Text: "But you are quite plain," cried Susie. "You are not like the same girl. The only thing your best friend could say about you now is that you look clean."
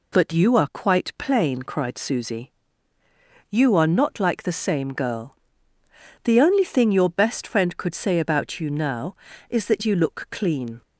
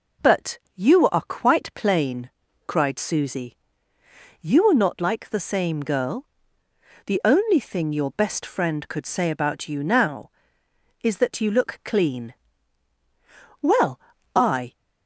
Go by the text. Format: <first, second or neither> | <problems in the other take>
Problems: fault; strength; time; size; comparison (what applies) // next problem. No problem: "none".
first | pauses between "But" and "you"; slight; at 0.5 s; 0.16 s long // goes on to say "Well I"; noticeable; from 13.6 s on; 1.1 s long